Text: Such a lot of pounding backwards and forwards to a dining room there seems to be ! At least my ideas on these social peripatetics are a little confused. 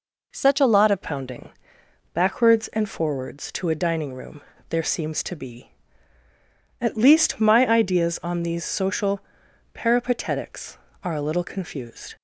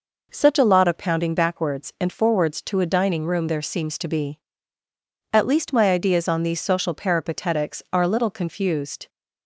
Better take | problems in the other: second | changes voice at "pounding"; from 1.0 s on; 11.1 s long // pauses between "pounding" and "backwards"; noticeable; at 1.5 s; 0.60 s long // pauses between "room" and "there"; slight; at 4.4 s; 0.26 s long // pauses between "social" and "peripatetics"; noticeable; at 9.2 s; 0.50 s long

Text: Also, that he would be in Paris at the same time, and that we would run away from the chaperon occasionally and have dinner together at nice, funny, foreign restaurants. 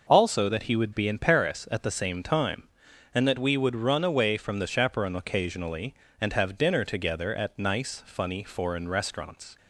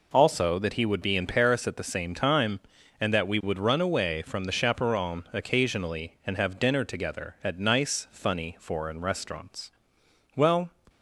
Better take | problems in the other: first | goes on to say "Well"; slight; from 10.3 s on; 0.38 s long

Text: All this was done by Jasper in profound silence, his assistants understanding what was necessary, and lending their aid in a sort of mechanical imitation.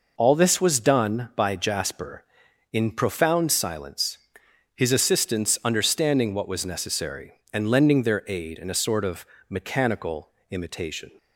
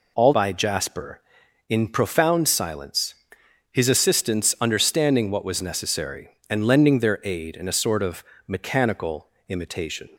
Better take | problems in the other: first | skips "this was done"; at 0.3 s // pauses between "of" and "mechanical"; slight; at 8.2 s; 0.24 s long; slight in the first // pauses between "mechanical" and "imitation"; slight; at 9.2 s; 0.22 s long; slight in the first

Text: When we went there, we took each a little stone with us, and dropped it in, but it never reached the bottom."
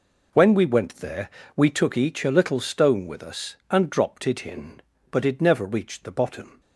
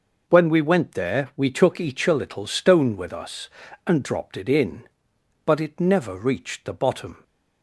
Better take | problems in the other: neither | none

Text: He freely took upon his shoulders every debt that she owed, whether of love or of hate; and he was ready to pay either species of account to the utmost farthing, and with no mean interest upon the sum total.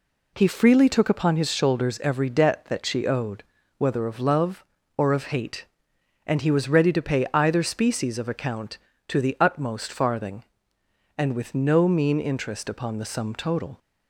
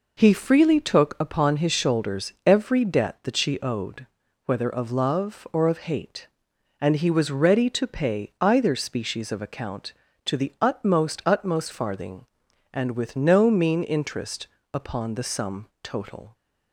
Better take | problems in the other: first | says "utmost" twice; at 11.2 s // pauses between "interest" and "upon"; slight; at 14.4 s; 0.26 s long // pauses between "sum" and "total"; slight; at 15.6 s; 0.15 s long

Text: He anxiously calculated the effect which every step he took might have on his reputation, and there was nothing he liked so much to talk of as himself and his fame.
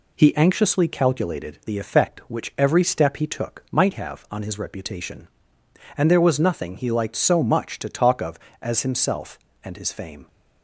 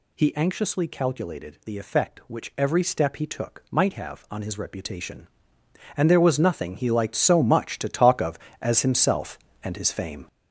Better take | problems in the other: first | gets louder; throughout; 7 dB

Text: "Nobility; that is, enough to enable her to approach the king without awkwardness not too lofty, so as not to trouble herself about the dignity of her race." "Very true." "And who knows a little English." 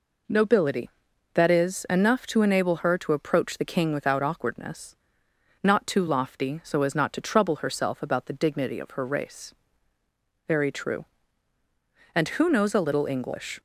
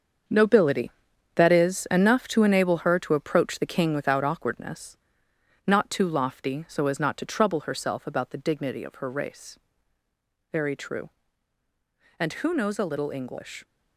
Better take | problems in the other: first | gets quieter; strong; throughout; 8.5 dB // pauses between "awkwardness" and "not"; noticeable; at 4.9 s; 0.70 s long; noticeable in the first

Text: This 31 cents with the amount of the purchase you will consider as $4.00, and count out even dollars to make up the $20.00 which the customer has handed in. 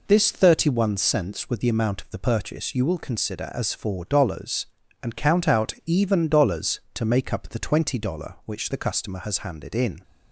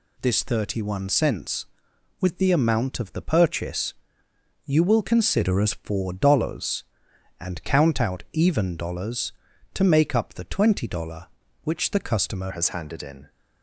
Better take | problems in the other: first | pauses between "purchase" and "you"; noticeable; at 3.9 s; 0.72 s long // changes voice at "has"; from 12.5 s on; 0.7 s long

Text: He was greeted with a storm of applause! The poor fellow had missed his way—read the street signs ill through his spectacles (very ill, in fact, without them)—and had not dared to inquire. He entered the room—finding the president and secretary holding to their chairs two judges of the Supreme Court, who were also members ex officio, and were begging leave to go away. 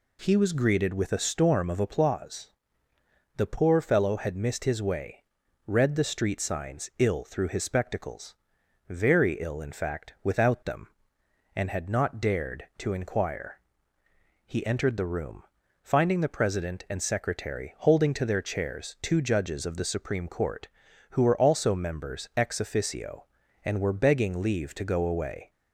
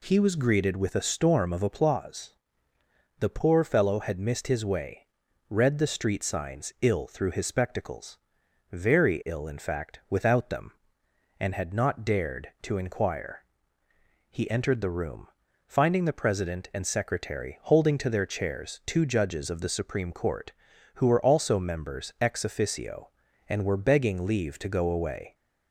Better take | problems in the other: neither | none

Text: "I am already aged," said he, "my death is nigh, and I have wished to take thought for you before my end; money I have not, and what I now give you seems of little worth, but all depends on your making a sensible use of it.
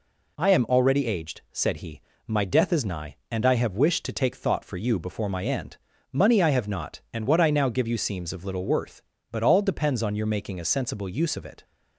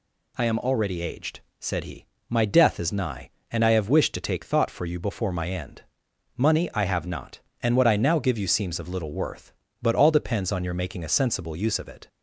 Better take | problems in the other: neither | none

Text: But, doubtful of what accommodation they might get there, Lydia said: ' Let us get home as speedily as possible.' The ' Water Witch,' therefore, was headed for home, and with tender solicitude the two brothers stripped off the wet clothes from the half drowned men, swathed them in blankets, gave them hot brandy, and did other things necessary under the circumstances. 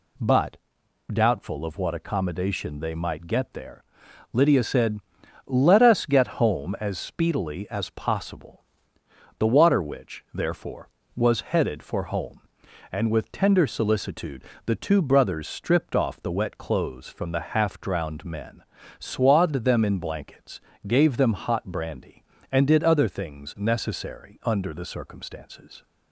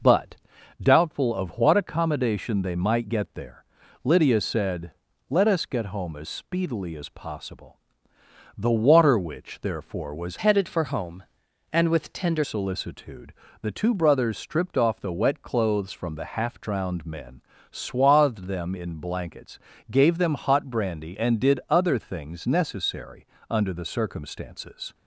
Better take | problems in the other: first | changes voice from "headed" to "tender"; from 10.3 to 12.4 s; 2.1 s long // pauses between "solicitude" and "the"; slight; at 13.3 s; 0.30 s long; slight in the first // pauses between "necessary" and "under"; slight; at 23.2 s; 0.24 s long

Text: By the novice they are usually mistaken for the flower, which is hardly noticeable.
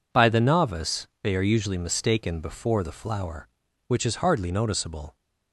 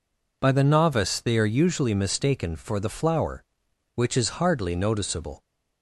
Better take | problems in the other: second | pauses between "novice" and "they"; slight; at 1.0 s; 0.16 s long // says "before" for "for"; at 2.4 s

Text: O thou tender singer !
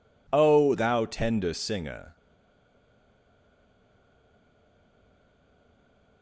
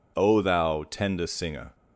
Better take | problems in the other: second | stays silent after the last word; strong; from 2.1 s on; 4.1 s long

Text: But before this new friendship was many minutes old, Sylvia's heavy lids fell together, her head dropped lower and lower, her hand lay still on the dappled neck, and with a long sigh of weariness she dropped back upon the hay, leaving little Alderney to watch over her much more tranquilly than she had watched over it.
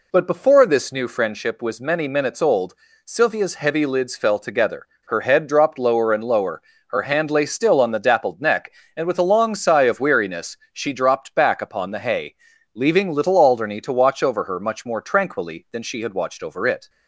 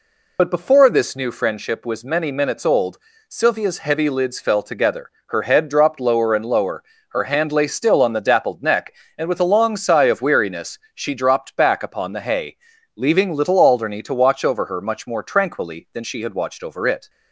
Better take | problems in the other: first | loses the start of "But"; at 0.3 s; 50 ms // pauses between "weariness" and "she"; slight; at 10.7 s; 0.16 s long; slight in the first

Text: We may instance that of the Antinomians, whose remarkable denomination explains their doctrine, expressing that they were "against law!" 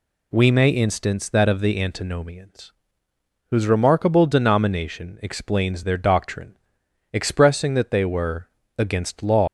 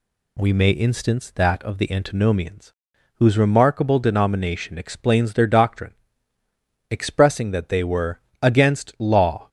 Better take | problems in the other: second | pauses between "were" and "against"; slight; at 8.4 s; 0.32 s long; slight in the second // leaves "law" unfinished; at 9.4 s; 150 ms

